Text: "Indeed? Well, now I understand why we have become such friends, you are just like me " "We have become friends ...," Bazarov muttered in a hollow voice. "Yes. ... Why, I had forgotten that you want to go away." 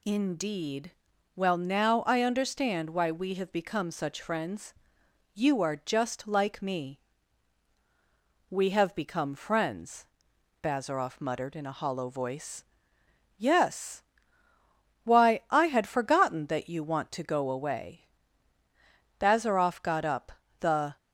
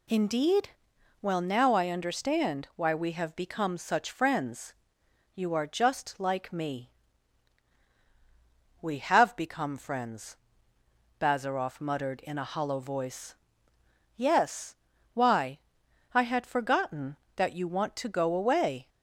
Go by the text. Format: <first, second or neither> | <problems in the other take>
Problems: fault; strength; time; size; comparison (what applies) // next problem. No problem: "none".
second | goes on to say "Bazarov got up The"; strong; from 19.2 s on; 1.7 s long